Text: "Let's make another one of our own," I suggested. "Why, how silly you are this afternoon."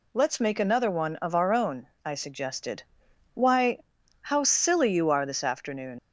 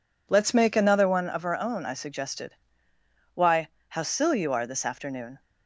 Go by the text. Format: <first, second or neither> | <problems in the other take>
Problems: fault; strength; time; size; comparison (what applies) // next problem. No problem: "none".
second | leaves "afternoon" unfinished; at 5.9 s; 90 ms